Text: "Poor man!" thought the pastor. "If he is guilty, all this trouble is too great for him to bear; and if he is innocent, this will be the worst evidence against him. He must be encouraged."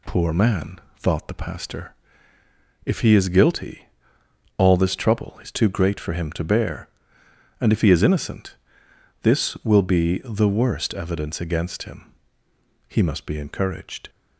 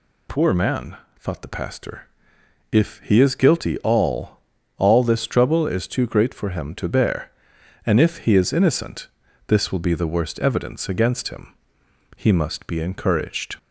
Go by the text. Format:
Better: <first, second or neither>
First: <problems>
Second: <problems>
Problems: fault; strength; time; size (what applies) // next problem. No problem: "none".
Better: first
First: none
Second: says "all" twice; at 4.7 s